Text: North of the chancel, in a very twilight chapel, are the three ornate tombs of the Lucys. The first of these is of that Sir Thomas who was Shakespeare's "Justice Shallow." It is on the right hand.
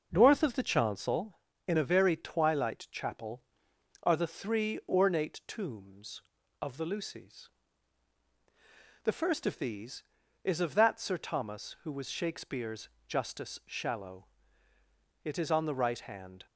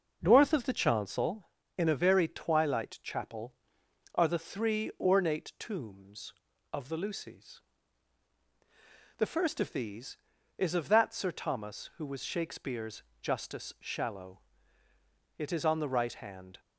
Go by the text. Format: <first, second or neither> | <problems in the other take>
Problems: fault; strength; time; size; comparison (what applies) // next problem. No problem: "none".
neither | pauses between "Shakespeare's" and "Justice"; slight; the same in both